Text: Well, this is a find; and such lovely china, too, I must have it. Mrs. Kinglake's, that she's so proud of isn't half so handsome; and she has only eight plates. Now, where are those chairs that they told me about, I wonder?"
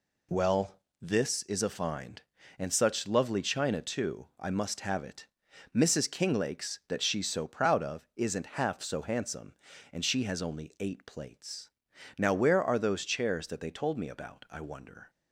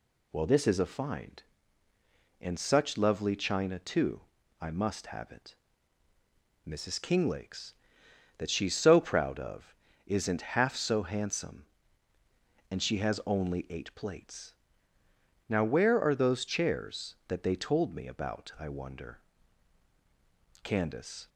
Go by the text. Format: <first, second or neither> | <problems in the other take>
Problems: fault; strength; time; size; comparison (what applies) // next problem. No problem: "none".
first | pauses between "of" and "isn't"; slight; at 9.7 s; 0.30 s long // goes on to say "Candace"; noticeable; from 20.6 s on; 0.66 s long